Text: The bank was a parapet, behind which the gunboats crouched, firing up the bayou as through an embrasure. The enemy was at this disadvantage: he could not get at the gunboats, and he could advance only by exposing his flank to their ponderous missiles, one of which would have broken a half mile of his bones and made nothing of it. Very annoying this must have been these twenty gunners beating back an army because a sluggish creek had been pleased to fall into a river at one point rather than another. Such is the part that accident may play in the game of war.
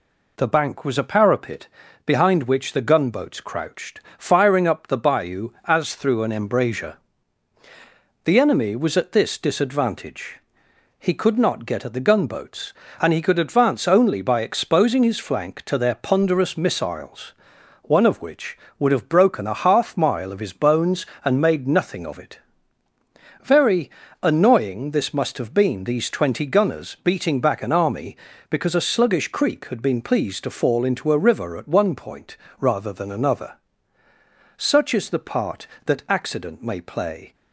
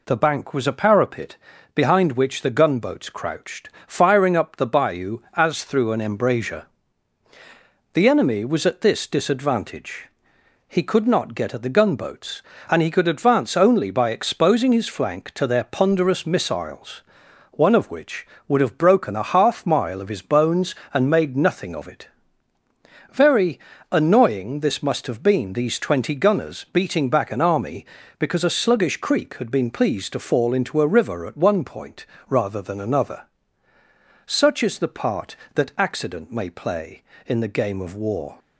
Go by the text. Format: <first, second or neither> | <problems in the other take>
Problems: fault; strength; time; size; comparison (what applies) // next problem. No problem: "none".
second | pauses between "Very" and "annoying"; slight; at 23.8 s; 0.32 s long; slight in the second // pauses between "point" and "rather"; slight; at 32.3 s; 0.20 s long; slight in the second // stops before "in the game of war"; at 37.3 s